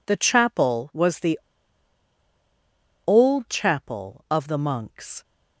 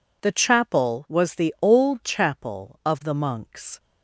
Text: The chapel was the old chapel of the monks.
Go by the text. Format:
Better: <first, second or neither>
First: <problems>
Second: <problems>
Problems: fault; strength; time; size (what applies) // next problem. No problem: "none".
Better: second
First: pauses between "the" and "old"; strong; at 1.3 s; 1.6 s long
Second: none